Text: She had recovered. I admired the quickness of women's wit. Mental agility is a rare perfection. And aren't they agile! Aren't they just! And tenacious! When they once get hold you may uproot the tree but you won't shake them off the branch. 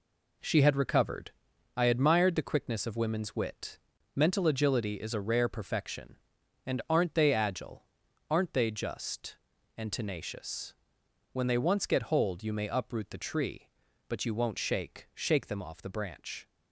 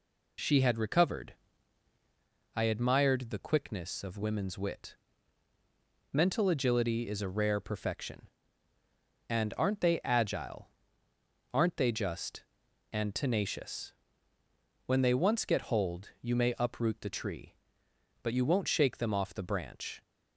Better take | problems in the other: second | says "shake" twice; at 15.1 s

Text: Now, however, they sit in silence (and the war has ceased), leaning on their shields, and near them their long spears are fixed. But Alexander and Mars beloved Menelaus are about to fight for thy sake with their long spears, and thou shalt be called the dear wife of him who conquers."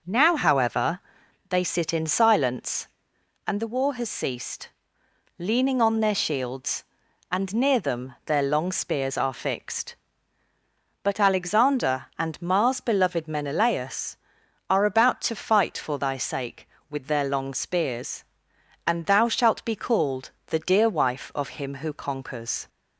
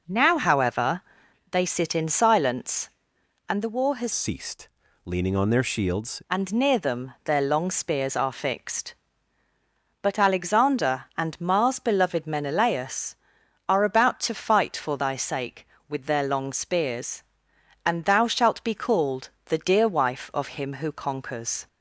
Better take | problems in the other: first | changes voice from "ceased" to "shields"; from 4.1 to 6.2 s; 2.1 s long // pauses between "called" and "the"; slight; at 19.2 s; 0.16 s long; slight in the first

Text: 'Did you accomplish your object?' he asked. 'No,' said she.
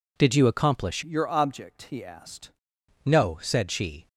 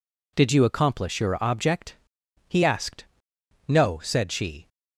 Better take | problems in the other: second | changes voice from "your" to "asked"; from 1.0 to 2.5 s; 1.5 s long

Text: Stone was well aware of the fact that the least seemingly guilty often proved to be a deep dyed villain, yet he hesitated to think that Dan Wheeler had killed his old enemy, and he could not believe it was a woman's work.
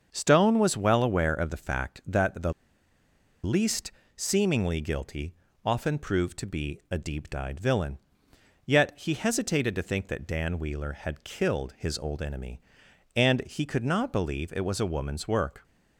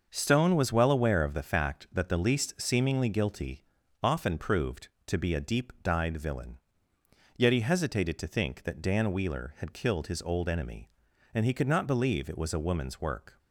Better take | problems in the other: second | starts louder than the rest; until 1.1 s; 6.5 dB; also in the second // pauses between "the" and "least"; noticeable; at 2.5 s; 0.91 s long // pauses between "least" and "seemingly"; slight; at 3.9 s; 0.24 s long // pauses between "guilty" and "often"; slight; at 5.3 s; 0.32 s long; also in the second

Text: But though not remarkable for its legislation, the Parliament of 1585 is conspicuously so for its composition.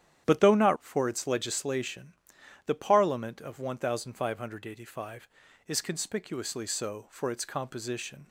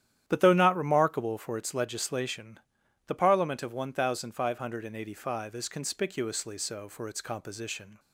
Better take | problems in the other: second | starts louder than the rest; strong; until 1.2 s; 10 dB; strong in the second // skips "remarkable"; at 0.7 s

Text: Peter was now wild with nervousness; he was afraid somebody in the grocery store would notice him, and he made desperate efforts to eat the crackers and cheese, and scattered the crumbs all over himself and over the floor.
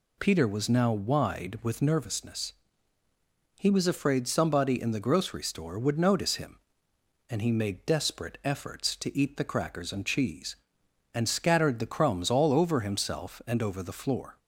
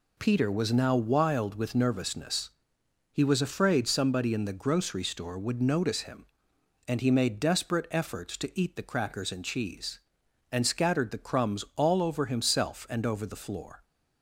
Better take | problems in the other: second | says "wide" for "wild"; at 0.9 s

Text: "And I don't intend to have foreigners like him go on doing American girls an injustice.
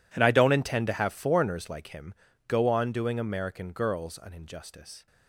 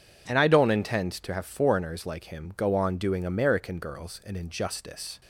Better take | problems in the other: second | gets quieter; strong; throughout; 19 dB // pauses between "him" and "go"; slight; at 2.1 s; 0.34 s long

